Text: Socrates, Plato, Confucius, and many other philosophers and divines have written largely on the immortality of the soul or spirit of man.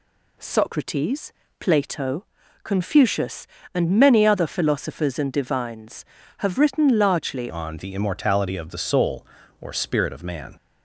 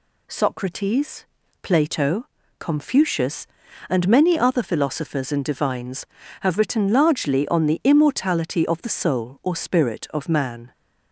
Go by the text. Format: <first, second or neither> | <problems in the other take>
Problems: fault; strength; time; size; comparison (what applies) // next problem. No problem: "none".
second | changes voice at "on"; from 7.4 s on; 3.1 s long